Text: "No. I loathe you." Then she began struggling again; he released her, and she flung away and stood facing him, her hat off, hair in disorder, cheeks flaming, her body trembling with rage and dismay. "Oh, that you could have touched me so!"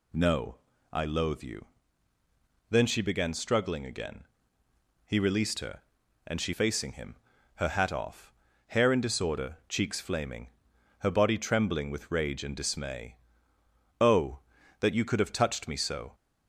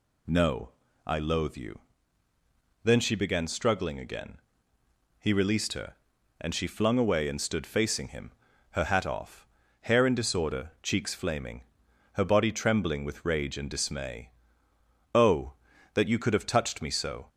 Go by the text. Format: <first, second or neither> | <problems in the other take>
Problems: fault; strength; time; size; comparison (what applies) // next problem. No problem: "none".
second | skips "flung away and stood"; at 6.5 s